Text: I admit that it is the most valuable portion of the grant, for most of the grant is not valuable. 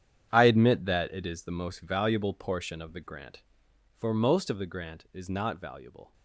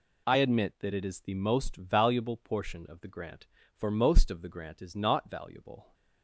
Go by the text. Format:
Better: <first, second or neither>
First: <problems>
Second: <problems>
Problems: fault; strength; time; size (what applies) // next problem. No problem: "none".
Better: second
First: gets quieter; strong; throughout; 13 dB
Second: none